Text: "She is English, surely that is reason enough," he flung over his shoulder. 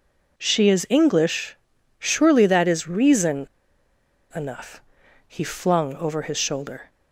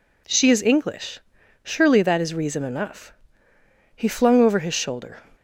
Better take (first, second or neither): second